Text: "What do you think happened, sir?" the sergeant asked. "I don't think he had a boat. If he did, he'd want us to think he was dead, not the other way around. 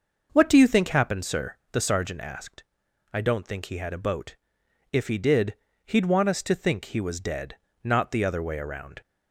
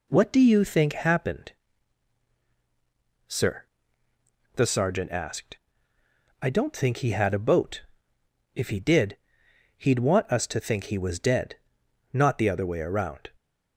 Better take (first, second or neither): neither